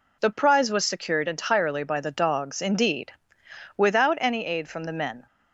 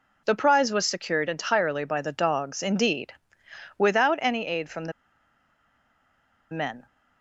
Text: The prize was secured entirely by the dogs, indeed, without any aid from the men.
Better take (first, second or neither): first